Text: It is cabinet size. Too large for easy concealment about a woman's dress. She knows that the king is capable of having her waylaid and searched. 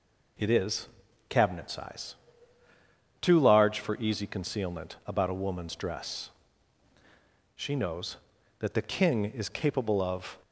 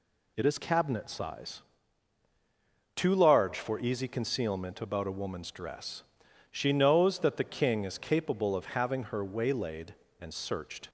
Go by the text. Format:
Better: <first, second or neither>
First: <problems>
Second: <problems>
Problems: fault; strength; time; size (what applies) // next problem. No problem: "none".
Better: second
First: pauses between "is" and "cabinet"; at 0.8 s; 0.42 s long // stops before "having her waylaid and searched"; at 10.4 s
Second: none